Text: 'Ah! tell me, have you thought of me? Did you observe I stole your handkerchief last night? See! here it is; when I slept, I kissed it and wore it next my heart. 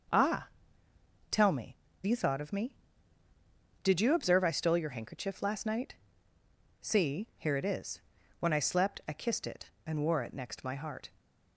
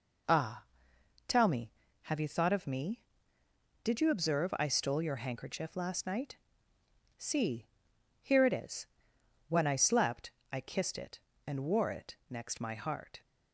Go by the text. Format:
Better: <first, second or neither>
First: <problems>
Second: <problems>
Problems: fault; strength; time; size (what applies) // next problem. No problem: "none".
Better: second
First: skips "have"; at 1.9 s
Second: none